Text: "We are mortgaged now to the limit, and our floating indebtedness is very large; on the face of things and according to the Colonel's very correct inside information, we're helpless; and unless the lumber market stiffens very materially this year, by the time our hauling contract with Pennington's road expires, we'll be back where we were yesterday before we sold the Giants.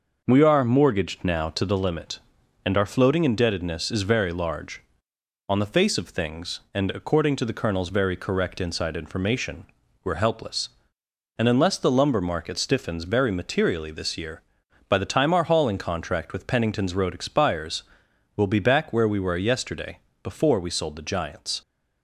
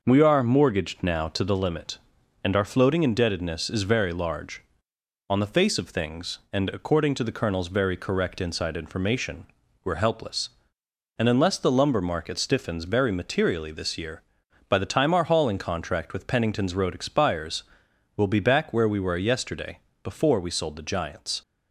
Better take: neither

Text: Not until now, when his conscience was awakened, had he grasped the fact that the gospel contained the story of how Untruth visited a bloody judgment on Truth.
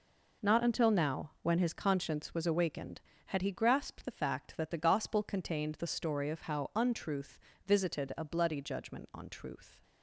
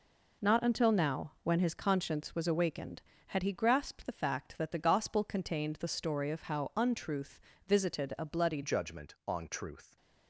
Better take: first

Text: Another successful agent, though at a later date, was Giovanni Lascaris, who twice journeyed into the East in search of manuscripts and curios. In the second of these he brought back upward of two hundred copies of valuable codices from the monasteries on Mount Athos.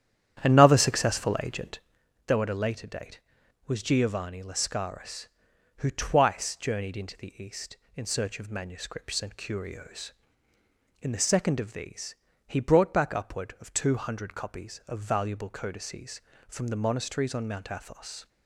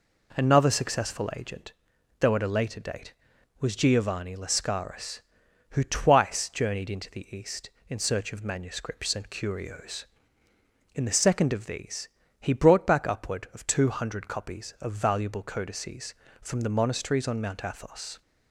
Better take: second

